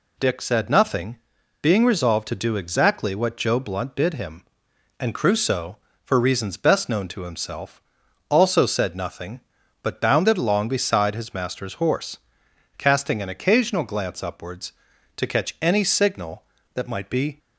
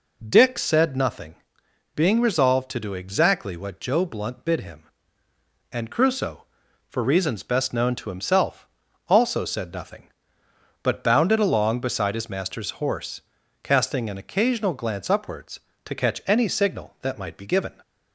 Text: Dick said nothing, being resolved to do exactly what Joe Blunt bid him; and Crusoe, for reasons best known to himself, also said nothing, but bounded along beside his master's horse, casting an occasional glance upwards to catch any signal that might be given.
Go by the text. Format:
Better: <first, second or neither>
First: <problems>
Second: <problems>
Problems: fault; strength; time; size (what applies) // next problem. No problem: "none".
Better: second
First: stops before "given"; at 17.3 s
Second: none